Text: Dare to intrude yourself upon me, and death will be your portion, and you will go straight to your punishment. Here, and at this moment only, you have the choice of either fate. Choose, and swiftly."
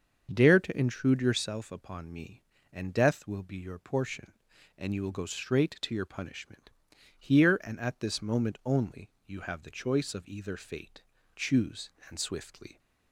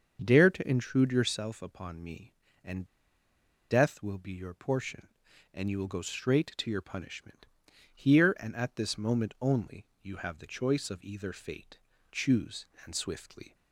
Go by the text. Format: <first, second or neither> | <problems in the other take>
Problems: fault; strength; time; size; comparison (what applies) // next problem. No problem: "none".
first | starts louder than the rest; until 1.2 s; 6.5 dB; also in the first // pauses between "and" and "death"; noticeable; at 2.8 s; 0.86 s long